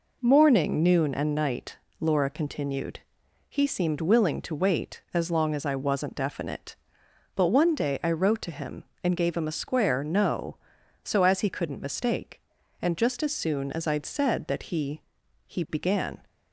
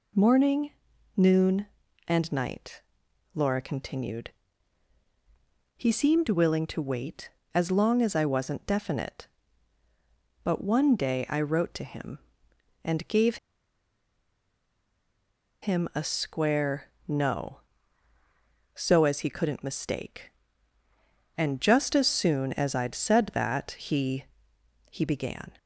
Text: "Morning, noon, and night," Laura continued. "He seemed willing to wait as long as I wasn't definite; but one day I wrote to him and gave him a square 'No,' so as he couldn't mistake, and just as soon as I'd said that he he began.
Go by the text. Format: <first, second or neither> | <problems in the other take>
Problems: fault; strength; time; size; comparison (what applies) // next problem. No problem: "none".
first | pauses between "gave" and "him"; strong; at 13.3 s; 2.2 s long // pauses between "square" and "No"; slight; at 16.9 s; 0.16 s long // pauses between "he" and "he"; noticeable; at 24.2 s; 0.66 s long; also in the first